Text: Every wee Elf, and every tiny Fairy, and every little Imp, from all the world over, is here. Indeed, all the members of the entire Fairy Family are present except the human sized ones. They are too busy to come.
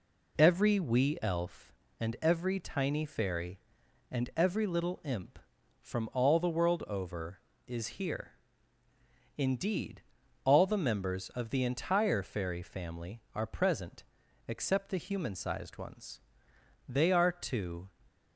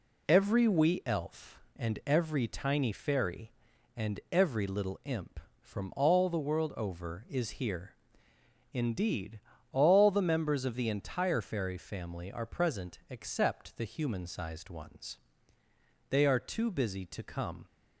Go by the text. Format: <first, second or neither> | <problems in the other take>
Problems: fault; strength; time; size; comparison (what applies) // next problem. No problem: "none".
second | pauses between "present" and "except"; at 14.0 s; 0.42 s long // stops before "busy to come"; at 18.0 s